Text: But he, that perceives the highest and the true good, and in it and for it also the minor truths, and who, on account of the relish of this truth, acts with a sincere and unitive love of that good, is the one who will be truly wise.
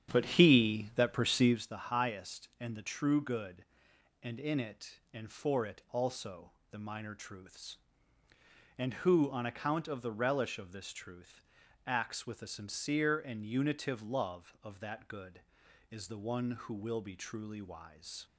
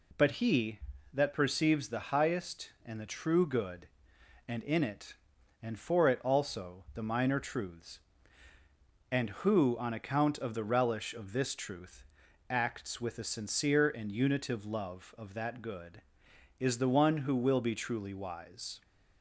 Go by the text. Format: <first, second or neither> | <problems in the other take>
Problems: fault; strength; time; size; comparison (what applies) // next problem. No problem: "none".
second | starts louder than the rest; strong; until 1.6 s; 9 dB // pauses between "also" and "the"; slight; at 6.5 s; 0.20 s long